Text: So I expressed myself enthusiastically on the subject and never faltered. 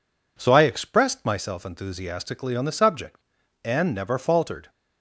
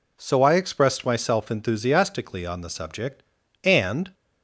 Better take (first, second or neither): first